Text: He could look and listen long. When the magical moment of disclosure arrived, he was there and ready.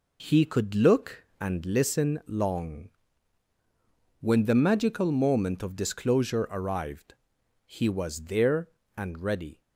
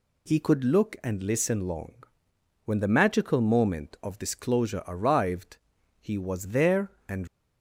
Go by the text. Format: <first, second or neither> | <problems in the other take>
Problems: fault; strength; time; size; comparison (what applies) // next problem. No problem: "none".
first | stops before "ready"; at 7.2 s